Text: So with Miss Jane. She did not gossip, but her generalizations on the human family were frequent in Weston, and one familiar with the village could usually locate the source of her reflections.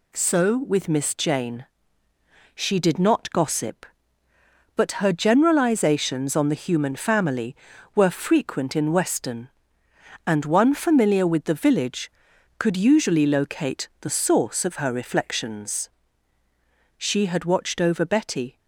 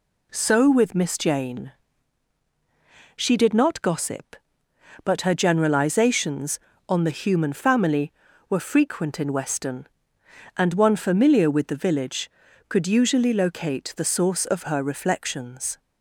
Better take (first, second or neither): second